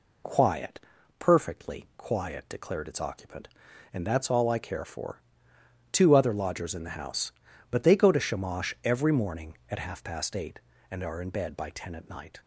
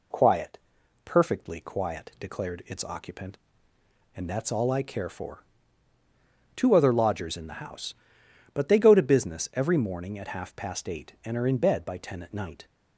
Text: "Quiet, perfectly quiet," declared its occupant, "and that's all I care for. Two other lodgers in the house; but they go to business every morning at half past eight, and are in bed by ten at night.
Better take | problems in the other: second | says "shamash" for "business"; at 8.1 s

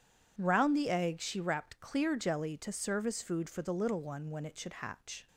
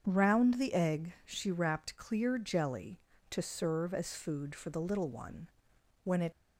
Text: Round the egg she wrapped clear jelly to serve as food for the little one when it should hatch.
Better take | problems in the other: first | starts louder than the rest; strong; until 1.0 s; 7.5 dB // pauses between "one" and "when"; noticeable; at 5.4 s; 0.54 s long // stops before "should hatch"; at 6.3 s

